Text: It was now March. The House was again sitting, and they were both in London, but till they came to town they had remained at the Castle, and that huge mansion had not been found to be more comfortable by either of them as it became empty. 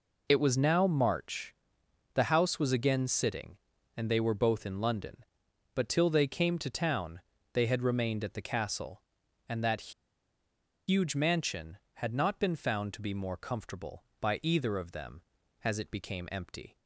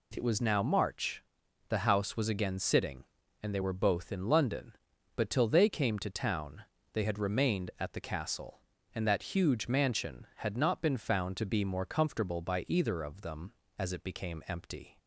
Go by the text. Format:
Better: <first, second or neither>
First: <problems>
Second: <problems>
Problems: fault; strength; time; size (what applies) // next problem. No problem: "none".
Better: second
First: pauses between "town" and "they"; slight; at 7.2 s; 0.32 s long // pauses between "that" and "huge"; noticeable; at 9.9 s; 0.96 s long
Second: pauses between "town" and "they"; slight; at 6.6 s; 0.28 s long